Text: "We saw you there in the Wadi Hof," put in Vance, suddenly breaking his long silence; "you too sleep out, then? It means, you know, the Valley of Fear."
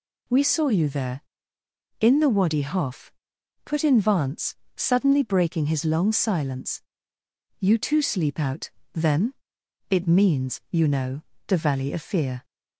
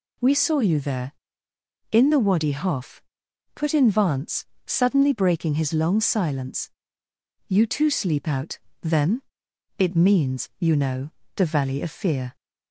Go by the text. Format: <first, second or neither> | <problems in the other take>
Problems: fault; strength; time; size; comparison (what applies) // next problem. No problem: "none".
neither | none